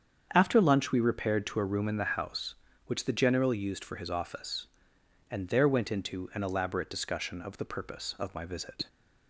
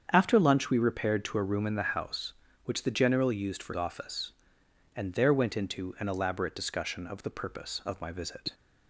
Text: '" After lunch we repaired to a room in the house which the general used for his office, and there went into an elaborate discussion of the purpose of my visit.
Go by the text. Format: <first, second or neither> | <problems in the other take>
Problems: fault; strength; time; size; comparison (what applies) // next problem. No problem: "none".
first | starts louder than the rest; strong; until 1.0 s; 7.5 dB; strong in the first // skips "his"; at 3.7 s